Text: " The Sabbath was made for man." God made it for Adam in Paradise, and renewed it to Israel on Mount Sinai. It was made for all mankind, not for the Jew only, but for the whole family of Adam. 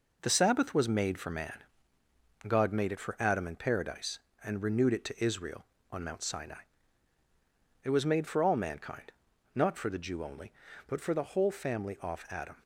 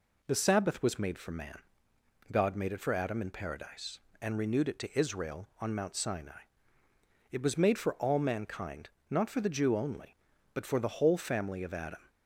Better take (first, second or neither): second